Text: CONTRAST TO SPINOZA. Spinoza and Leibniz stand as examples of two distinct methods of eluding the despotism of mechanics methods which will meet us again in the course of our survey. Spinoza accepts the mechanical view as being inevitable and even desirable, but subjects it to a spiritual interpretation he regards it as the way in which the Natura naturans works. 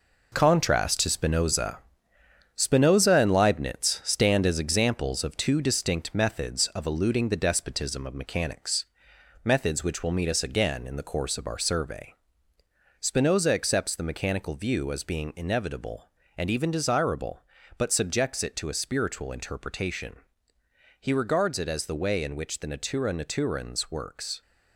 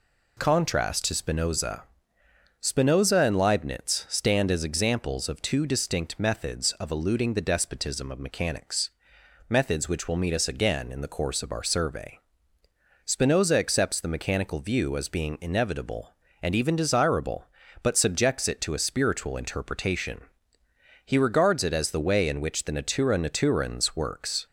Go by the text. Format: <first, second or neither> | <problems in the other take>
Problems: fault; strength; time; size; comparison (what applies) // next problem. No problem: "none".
second | gets quieter; strong; throughout; 7.5 dB // pauses between "mechanics" and "methods"; noticeable; at 8.8 s; 0.60 s long; noticeable in the second // pauses between "interpretation" and "he"; noticeable; at 20.1 s; 0.84 s long; noticeable in the second